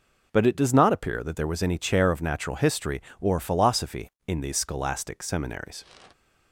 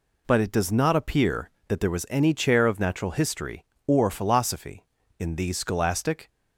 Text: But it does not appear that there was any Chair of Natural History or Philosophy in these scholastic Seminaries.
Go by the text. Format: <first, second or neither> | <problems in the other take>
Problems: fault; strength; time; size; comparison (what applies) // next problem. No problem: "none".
first | stops before "Seminaries"; at 6.2 s